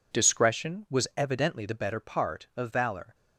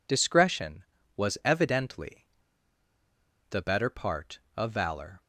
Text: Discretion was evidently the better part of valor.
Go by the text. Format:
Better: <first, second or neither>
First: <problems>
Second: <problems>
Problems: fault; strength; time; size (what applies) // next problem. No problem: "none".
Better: first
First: none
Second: pauses between "evidently" and "the"; strong; at 2.2 s; 1.2 s long